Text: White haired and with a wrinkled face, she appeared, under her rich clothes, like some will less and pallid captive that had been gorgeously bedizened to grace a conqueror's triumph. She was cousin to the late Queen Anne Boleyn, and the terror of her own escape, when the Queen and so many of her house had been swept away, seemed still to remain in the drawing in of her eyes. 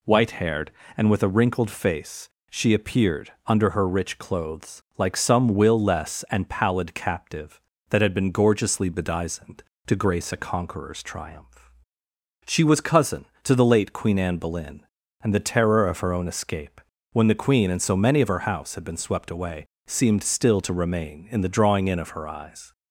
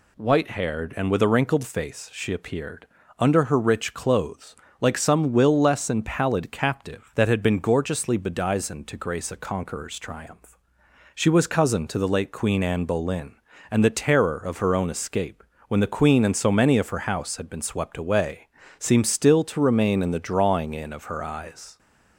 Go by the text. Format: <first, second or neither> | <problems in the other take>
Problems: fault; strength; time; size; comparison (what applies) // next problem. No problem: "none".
neither | none